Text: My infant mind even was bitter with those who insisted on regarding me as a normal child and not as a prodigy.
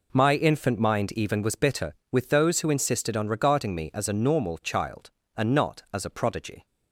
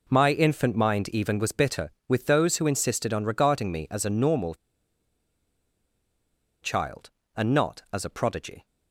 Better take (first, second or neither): first